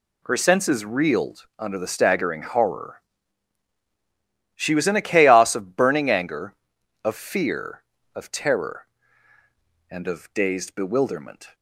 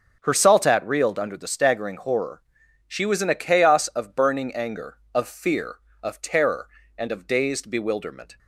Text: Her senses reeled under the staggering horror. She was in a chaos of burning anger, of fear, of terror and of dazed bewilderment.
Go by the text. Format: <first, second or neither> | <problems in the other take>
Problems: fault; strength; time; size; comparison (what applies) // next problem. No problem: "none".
first | says "saltat" for "senses"; at 0.3 s